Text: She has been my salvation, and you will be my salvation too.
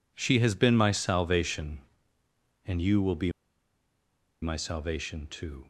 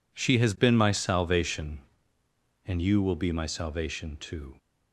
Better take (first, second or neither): second